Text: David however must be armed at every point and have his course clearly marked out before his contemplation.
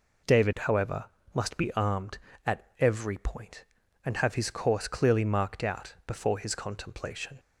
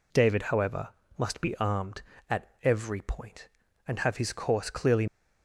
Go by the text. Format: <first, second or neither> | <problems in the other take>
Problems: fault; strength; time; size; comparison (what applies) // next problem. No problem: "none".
first | pauses between "however" and "must"; slight; at 0.8 s; 0.30 s long; slight in the first // stops before "marked out before his contemplation"; at 5.0 s